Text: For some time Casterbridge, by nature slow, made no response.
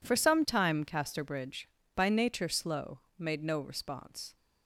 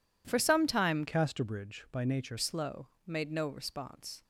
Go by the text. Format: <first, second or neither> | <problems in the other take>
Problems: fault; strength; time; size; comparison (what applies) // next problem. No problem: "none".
first | changes voice from "Casterbridge" to "nature"; from 1.0 to 2.3 s; 1.3 s long